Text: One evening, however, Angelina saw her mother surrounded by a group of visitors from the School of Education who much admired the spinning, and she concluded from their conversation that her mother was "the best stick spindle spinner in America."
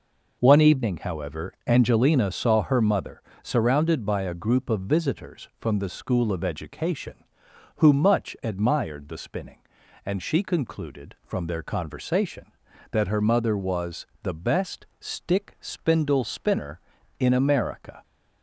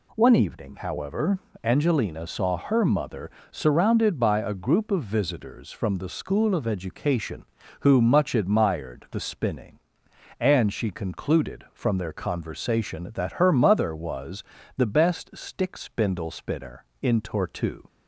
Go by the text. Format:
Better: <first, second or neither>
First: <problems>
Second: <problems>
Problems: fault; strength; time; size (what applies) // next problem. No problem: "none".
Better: first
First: pauses between "mother" and "surrounded"; slight; at 3.2 s; 0.20 s long // pauses between "was" and "the"; slight; at 14.0 s; 0.16 s long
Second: pauses between "mother" and "surrounded"; slight; at 3.2 s; 0.22 s long // pauses between "was" and "the"; slight; at 14.4 s; 0.36 s long // says "Tortue" for "America"; at 17.1 s